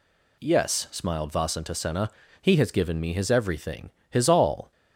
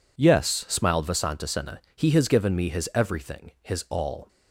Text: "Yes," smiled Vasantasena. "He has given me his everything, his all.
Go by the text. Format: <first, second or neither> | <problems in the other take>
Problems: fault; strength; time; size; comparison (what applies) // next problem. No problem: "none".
neither | none